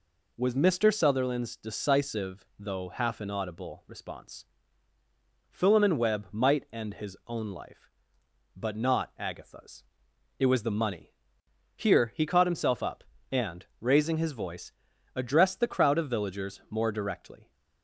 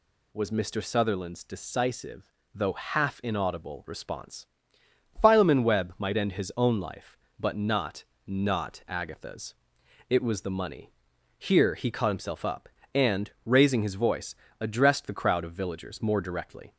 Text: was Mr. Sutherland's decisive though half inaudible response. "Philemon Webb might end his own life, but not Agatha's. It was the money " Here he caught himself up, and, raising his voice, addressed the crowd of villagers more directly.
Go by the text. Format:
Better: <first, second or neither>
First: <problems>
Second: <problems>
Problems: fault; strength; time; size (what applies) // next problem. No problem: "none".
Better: first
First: none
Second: pauses between "decisive" and "though"; slight; at 2.2 s; 0.28 s long // says "not" twice; at 8.2 s